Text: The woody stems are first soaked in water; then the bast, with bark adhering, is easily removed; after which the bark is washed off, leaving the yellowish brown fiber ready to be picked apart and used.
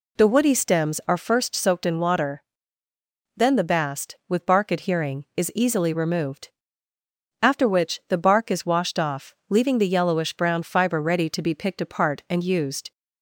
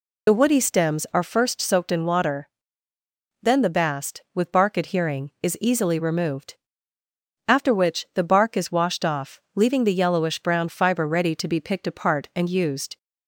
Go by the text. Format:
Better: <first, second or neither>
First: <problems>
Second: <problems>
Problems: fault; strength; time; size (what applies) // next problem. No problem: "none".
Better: first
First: none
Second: loses the start of "The"; at 0.2 s; 40 ms